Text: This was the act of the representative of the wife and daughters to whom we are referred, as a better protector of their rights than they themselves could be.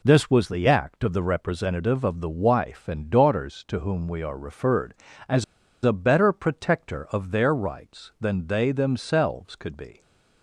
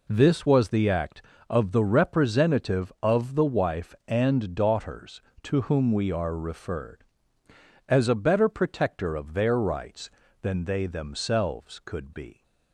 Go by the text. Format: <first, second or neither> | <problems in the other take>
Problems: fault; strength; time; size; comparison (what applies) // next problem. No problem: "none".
second | pauses between "as" and "a"; at 5.4 s; 0.40 s long